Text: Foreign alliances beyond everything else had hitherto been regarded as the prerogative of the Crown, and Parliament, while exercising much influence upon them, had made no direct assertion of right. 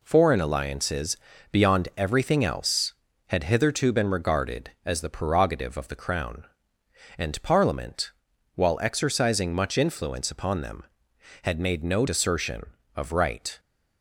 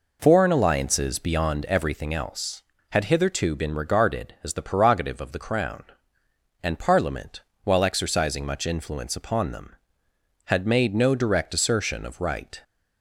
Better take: second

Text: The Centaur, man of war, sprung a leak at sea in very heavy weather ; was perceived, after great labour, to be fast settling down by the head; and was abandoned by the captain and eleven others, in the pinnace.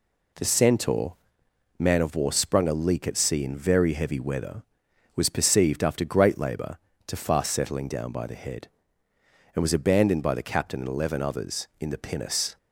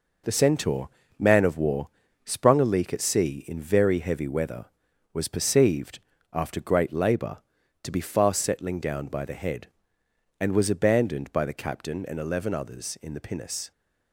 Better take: second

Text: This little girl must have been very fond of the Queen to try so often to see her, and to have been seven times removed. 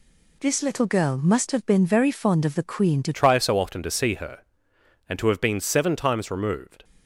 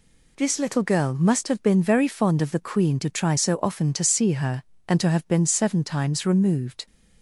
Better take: second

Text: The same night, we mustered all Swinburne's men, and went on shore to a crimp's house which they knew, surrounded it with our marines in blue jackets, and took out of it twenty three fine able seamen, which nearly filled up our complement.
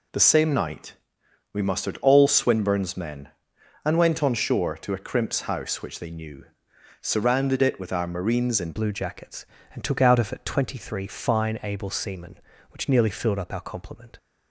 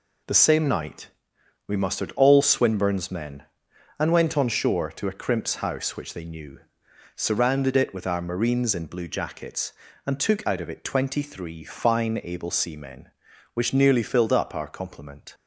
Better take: second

